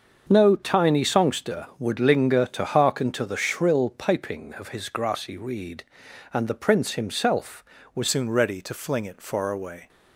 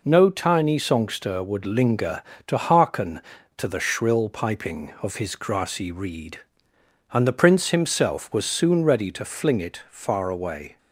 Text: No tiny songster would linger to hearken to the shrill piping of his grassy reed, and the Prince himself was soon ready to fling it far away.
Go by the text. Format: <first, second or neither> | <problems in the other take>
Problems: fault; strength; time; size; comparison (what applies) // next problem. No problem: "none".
second | starts louder than the rest; until 1.3 s; 6.5 dB // changes voice at "soon"; from 8.0 s on; 1.8 s long